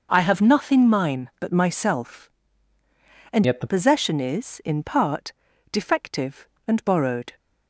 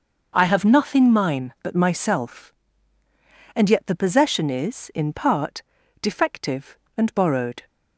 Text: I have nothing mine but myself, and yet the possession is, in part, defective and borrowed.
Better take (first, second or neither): second